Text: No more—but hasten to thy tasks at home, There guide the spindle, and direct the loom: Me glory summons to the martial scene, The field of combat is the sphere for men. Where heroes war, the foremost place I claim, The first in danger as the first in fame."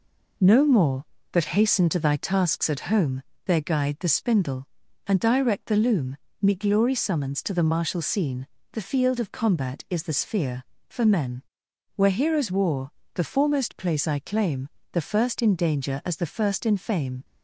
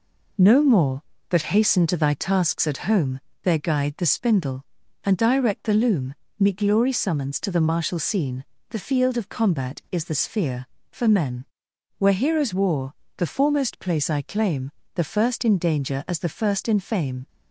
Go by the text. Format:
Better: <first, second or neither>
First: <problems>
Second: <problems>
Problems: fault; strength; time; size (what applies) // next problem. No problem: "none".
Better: neither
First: none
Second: none